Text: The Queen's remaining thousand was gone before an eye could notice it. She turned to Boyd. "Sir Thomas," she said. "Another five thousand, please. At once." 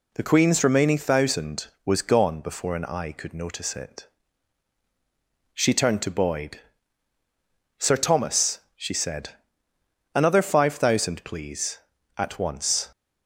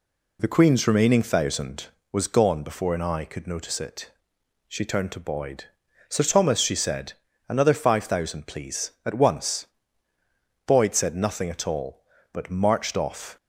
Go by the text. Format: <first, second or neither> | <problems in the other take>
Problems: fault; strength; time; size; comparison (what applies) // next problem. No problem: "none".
first | goes on to say "Boyd said nothing at all but marched off"; strong; from 10.6 s on; 2.7 s long